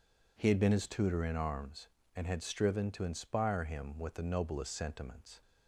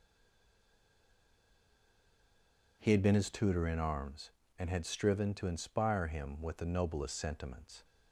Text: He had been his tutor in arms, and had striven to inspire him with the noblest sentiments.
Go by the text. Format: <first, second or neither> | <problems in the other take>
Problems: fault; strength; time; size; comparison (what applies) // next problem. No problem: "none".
first | stays silent before the first word; strong; until 2.8 s; 2.8 s long